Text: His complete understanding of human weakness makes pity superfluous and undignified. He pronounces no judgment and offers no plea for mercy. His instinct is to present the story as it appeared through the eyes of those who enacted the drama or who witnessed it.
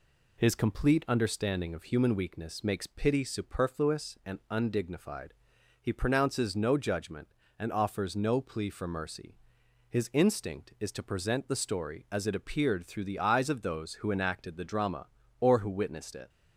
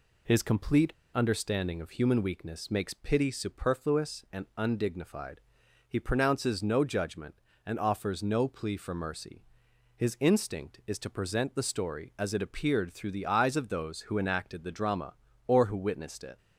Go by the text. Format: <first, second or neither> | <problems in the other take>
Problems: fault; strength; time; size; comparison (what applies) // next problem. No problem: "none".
first | pauses between "complete" and "understanding"; slight; at 0.9 s; 0.22 s long